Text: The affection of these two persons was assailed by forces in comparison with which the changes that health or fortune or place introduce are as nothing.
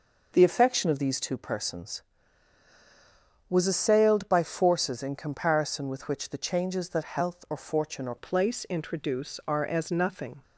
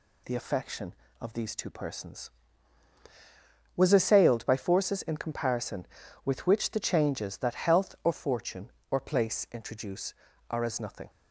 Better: second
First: changes voice at "place"; from 8.1 s on; 2.3 s long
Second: none

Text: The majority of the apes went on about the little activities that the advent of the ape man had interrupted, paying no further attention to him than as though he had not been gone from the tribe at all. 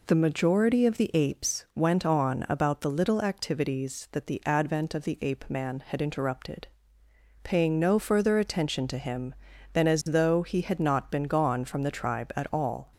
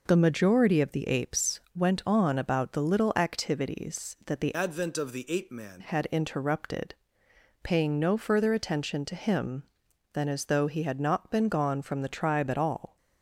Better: first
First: none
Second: pauses between "apes" and "went"; slight; at 1.5 s; 0.16 s long // changes voice from "advent" to "man"; from 4.5 to 5.8 s; 1.3 s long

